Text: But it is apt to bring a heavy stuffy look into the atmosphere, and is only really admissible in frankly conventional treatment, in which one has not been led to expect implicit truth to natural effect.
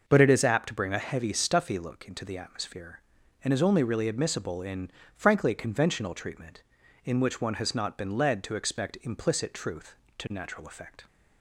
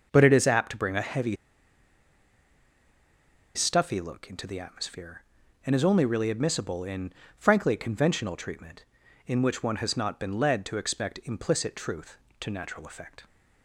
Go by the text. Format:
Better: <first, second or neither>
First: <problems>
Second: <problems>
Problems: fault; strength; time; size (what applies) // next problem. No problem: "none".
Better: first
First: pauses between "in" and "frankly"; slight; at 4.9 s; 0.26 s long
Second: pauses between "heavy" and "stuffy"; strong; at 1.3 s; 2.1 s long // pauses between "in" and "frankly"; slight; at 7.1 s; 0.26 s long